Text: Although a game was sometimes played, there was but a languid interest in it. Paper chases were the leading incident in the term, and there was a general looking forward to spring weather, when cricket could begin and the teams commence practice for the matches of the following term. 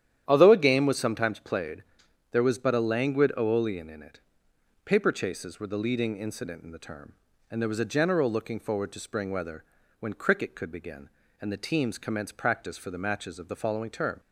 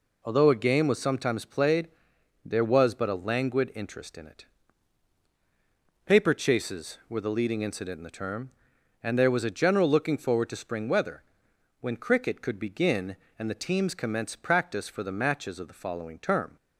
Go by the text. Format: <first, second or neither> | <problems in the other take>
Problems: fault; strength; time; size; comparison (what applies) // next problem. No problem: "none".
second | starts louder than the rest; strong; until 1.2 s; 10.5 dB // says "aeolian" for "interest"; at 3.3 s